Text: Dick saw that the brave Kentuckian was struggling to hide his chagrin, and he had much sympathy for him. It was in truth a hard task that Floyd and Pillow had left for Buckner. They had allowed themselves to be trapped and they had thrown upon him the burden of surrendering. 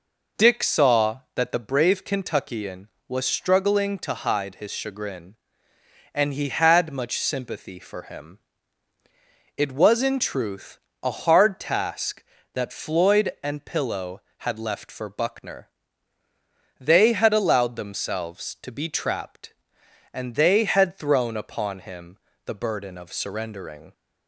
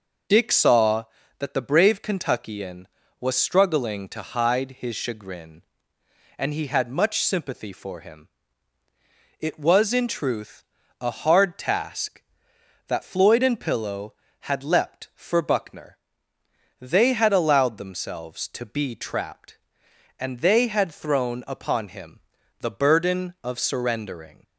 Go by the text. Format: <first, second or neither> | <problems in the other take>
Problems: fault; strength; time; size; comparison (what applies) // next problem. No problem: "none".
first | pauses between "truth" and "a"; at 10.6 s; 0.38 s long; slight in the first // says "leapt" for "left"; at 14.6 s // pauses between "him" and "the"; at 22.2 s; 0.40 s long; slight in the first